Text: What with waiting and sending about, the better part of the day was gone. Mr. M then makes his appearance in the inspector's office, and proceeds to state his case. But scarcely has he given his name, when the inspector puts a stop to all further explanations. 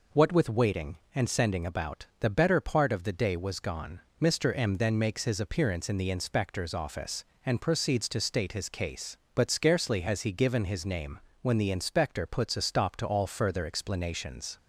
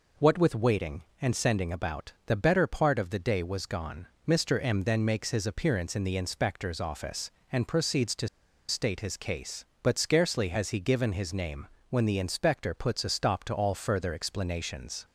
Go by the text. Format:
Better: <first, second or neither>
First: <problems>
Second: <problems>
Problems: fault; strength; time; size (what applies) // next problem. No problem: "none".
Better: first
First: none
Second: pauses between "to" and "state"; at 8.2 s; 0.40 s long